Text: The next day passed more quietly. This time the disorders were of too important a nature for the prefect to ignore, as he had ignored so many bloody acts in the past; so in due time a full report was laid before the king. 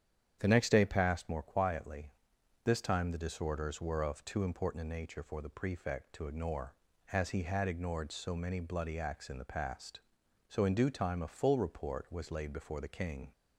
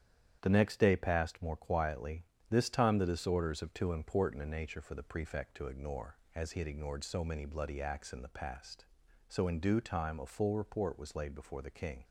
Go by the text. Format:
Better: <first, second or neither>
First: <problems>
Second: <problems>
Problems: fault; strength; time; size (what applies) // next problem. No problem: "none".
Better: first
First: starts louder than the rest; strong; until 1.4 s; 9 dB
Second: starts louder than the rest; strong; until 1.4 s; 9.5 dB // skips "were"; at 3.6 s